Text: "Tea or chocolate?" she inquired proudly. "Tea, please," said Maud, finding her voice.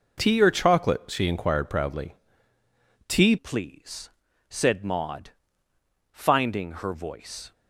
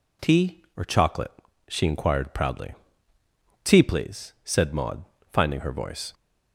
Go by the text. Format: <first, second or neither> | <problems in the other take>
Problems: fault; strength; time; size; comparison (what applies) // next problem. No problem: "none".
second | changes voice at "please"; from 3.3 s on; 4.2 s long